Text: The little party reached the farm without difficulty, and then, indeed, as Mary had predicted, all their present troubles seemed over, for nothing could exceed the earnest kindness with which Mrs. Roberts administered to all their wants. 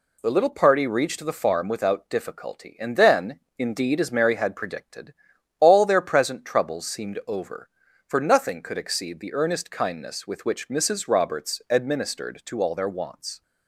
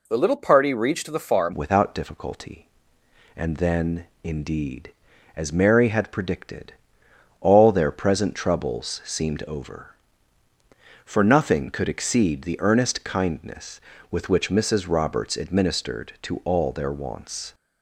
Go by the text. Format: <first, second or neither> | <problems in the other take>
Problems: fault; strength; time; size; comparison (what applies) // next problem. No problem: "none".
first | changes voice at "without"; from 1.5 s on; 16.0 s long